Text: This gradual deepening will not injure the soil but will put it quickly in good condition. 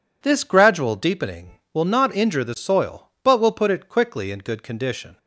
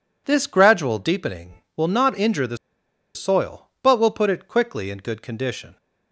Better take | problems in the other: first | pauses between "the" and "soil"; noticeable; at 2.5 s; 0.57 s long

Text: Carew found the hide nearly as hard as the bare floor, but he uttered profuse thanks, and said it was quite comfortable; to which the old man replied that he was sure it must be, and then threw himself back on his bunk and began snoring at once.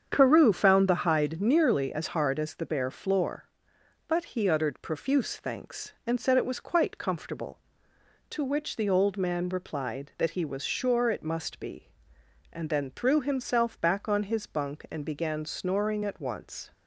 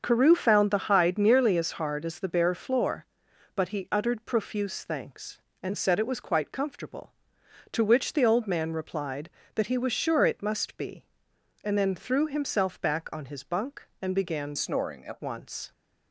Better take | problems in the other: first | starts louder than the rest; until 1.0 s; 6.5 dB; strong in the first // changes voice from "snoring" to "at"; from 14.5 to 15.1 s; 0.6 s long

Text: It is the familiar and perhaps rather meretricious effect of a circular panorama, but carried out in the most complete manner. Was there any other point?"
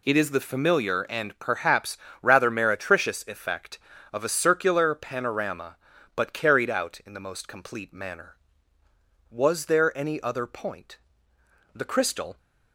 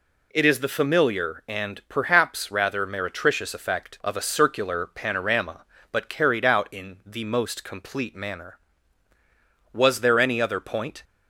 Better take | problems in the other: second | pauses between "perhaps" and "rather"; slight; at 1.9 s; 0.26 s long // goes on to say "The crystal"; noticeable; from 11.7 s on; 0.62 s long

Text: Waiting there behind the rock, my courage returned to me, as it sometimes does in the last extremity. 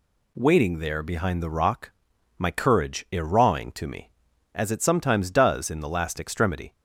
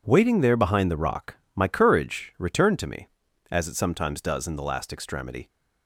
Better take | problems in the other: second | says "irawing" for "returned"; at 3.1 s

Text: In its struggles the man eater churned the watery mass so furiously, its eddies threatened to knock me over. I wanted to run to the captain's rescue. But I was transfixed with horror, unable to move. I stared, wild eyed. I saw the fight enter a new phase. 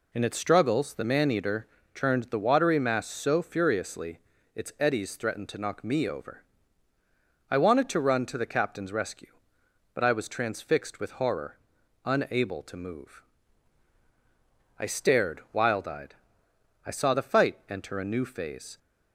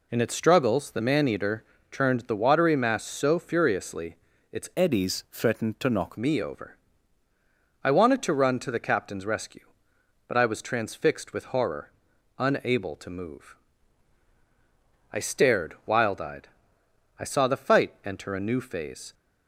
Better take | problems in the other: first | pauses between "eater" and "churned"; slight; at 1.6 s; 0.28 s long; slight in the first // changes voice from "eddies" to "knock"; from 4.7 to 6.1 s; 1.4 s long

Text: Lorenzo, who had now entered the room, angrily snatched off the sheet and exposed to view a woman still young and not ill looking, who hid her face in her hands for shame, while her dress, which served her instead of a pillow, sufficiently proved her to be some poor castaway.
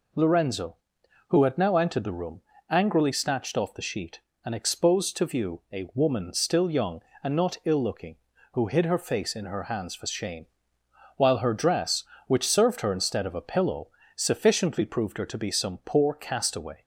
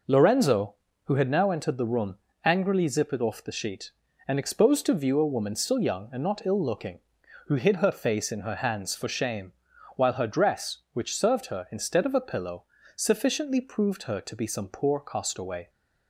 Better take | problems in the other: first | says "zippered" for "snatched"; at 2.8 s

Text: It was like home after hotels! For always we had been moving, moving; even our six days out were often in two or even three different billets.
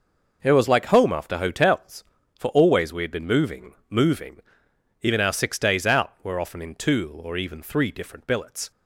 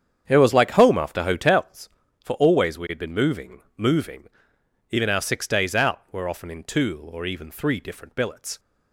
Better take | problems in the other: first | starts louder than the rest; strong; until 1.7 s; 8 dB

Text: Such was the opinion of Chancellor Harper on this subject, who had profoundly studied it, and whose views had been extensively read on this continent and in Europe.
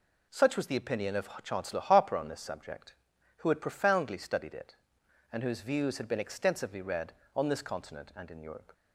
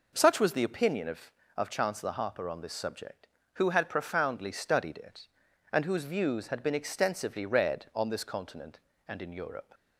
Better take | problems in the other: first | says "of" twice; at 1.5 s

